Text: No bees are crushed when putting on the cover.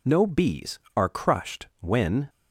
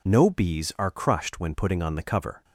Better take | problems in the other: second | stops before "putting on the cover"; at 2.2 s

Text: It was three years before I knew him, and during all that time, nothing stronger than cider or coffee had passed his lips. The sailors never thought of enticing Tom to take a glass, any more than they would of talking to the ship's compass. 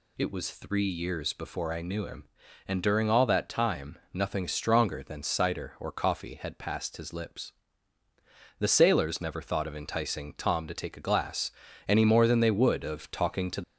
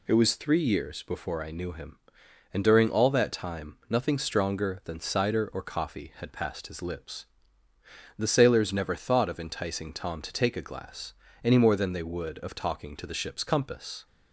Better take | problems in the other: second | stops before "the ship's compass"; at 13.6 s

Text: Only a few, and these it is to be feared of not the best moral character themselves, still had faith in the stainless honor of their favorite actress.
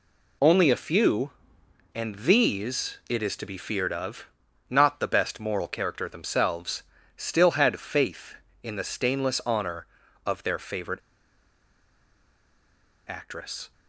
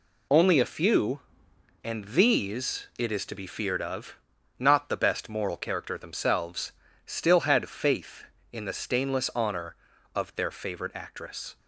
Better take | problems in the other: second | pauses between "of" and "not"; at 4.2 s; 0.42 s long; also in the second // pauses between "favorite" and "actress"; strong; at 10.9 s; 2.1 s long

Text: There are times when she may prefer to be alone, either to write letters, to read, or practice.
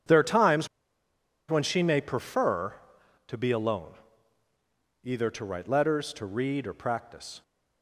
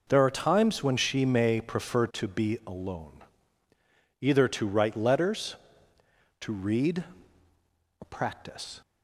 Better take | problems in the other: second | pauses between "times" and "when"; noticeable; at 0.6 s; 0.82 s long

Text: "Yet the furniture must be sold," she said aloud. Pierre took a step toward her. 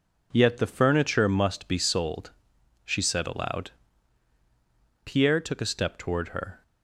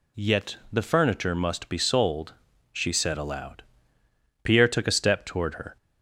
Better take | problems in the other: neither | none

